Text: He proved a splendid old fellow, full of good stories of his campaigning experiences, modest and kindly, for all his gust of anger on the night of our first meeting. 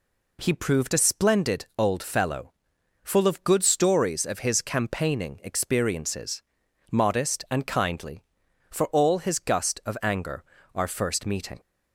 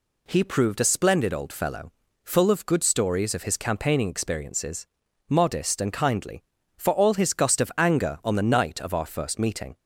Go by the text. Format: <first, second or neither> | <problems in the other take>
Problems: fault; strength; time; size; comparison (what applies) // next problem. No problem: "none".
second | skips "on the night of"; at 10.5 s